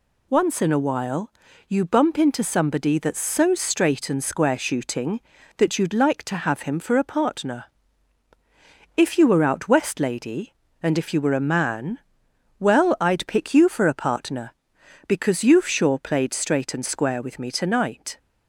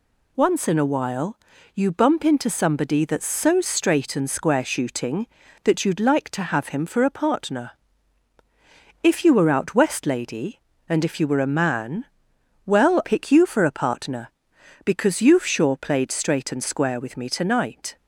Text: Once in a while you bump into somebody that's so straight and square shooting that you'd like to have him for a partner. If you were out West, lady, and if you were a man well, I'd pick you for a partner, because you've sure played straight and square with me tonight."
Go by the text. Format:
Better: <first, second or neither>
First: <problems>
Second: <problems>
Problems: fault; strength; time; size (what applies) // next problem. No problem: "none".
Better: first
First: pauses between "while" and "you"; at 1.3 s; 0.38 s long // pauses between "man" and "well"; noticeable; at 11.9 s; 0.62 s long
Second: pauses between "while" and "you"; at 1.3 s; 0.38 s long // pauses between "man" and "well"; noticeable; at 12.0 s; 0.62 s long // skips "I'd"; at 13.0 s